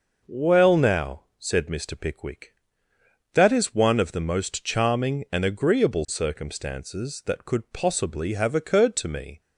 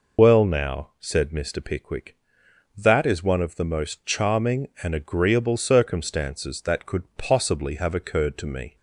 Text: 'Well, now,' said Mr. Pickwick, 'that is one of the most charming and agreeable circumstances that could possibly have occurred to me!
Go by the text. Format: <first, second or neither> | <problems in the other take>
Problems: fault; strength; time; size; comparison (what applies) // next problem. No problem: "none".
first | loses the start of "Well"; at 0.1 s; 65 ms